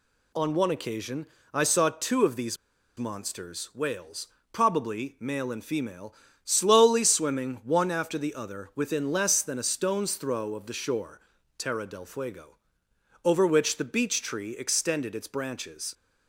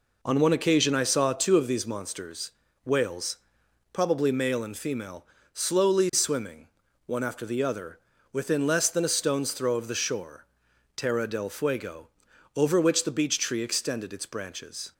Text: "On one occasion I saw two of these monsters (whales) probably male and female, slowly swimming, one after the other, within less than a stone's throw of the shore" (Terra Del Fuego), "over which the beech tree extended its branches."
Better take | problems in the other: second | pauses between "occasion" and "I"; slight; at 1.2 s; 0.26 s long // pauses between "these" and "monsters"; at 2.5 s; 0.40 s long

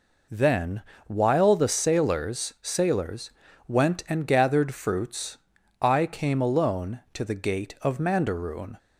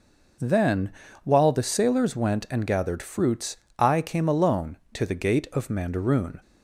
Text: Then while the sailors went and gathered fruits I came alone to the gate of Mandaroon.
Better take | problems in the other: second | pauses between "Then" and "while"; slight; at 0.8 s; 0.24 s long; slight in the second // says "sailors" twice; at 2.6 s // pauses between "fruits" and "I"; noticeable; at 5.3 s; 0.46 s long; slight in the second

